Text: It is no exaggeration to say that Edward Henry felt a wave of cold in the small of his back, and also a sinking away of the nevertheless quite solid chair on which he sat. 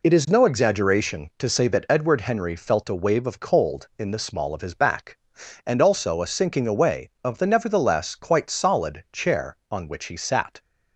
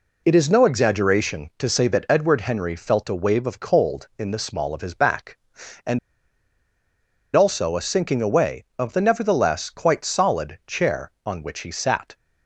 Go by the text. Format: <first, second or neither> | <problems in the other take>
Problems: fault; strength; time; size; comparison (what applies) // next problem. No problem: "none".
first | pauses between "and" and "also"; strong; at 5.9 s; 1.3 s long